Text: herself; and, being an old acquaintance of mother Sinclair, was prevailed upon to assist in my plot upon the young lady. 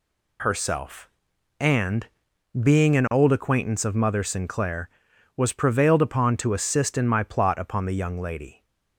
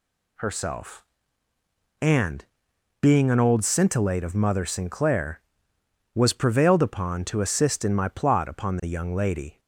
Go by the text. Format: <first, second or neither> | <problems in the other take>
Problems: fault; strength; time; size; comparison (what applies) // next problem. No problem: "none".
first | says "scintillate" for "acquaintance"; at 3.6 s